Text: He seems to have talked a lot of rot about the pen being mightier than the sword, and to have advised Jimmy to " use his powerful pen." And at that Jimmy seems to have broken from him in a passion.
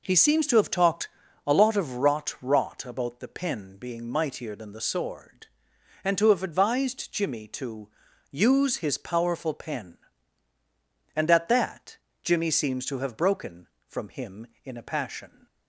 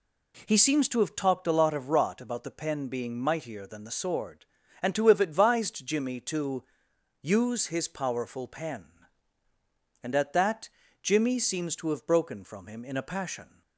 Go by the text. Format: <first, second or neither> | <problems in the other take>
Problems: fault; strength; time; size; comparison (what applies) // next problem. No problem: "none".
second | pauses between "talked" and "a"; at 1.0 s; 0.38 s long // says "rot" twice; at 2.4 s // pauses between "that" and "Jimmy"; slight; at 11.9 s; 0.26 s long; slight in the second